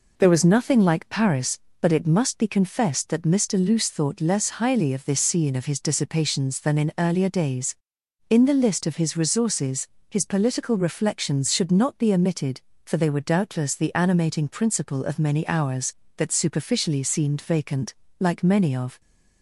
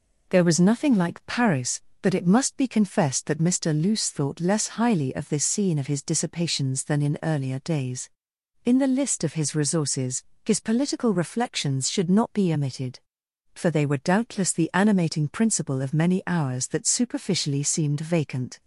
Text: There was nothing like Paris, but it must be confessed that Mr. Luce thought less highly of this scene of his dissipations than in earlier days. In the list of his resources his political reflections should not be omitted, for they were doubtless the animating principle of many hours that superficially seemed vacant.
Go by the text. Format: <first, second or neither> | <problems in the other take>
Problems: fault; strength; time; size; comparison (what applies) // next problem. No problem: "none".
second | pauses between "resources" and "his"; slight; at 9.8 s; 0.20 s long; slight in the second // goes on to say "Like many of"; noticeable; from 18.1 s on; 0.80 s long